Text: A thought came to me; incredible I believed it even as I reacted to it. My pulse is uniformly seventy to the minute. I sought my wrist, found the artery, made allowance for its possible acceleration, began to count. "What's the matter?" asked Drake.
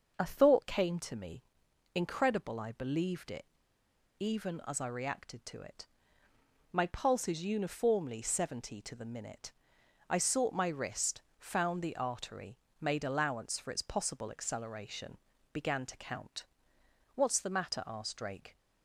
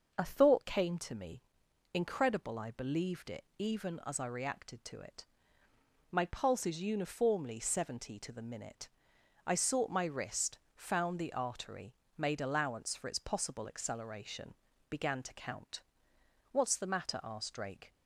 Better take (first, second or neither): second